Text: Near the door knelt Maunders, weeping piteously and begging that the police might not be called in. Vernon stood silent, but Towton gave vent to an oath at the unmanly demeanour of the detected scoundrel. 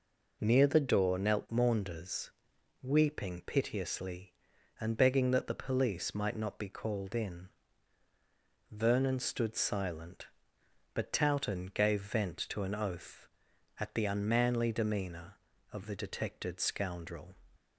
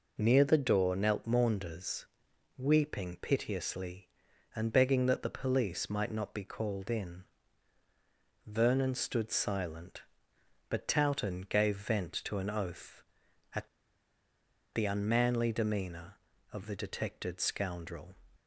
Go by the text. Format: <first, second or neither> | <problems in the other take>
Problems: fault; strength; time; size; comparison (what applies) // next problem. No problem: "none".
first | pauses between "at" and "the"; at 13.6 s; 1.0 s long